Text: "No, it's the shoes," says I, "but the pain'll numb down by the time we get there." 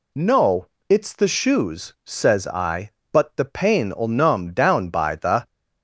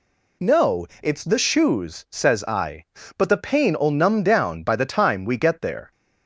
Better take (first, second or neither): second